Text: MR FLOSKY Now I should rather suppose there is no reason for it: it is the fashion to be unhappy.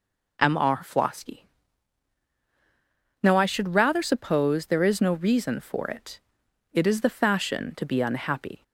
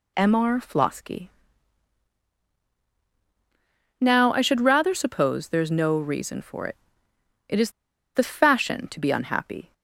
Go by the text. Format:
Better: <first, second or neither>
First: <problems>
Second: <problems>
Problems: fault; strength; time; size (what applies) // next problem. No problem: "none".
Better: first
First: pauses between "FLOSKY" and "Now"; strong; at 1.4 s; 1.7 s long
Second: pauses between "FLOSKY" and "Now"; strong; at 1.2 s; 2.6 s long // pauses between "is" and "the"; at 7.6 s; 0.45 s long